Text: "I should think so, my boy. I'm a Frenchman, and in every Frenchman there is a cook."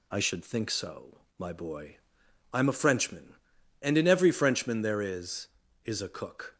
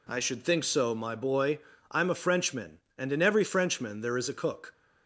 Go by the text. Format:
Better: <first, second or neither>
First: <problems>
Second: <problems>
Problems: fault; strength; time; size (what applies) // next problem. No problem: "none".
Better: second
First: says "is" twice; at 5.8 s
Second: none